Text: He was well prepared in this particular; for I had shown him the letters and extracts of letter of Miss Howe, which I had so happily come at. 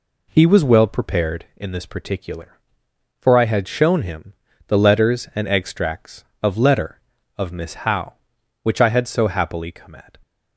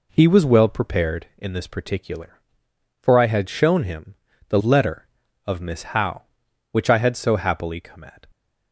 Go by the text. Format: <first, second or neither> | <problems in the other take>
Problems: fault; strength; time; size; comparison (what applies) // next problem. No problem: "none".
first | pauses between "him" and "the"; slight; at 4.1 s; 0.32 s long; slight in the first // skips "letters and extracts of"; at 4.6 s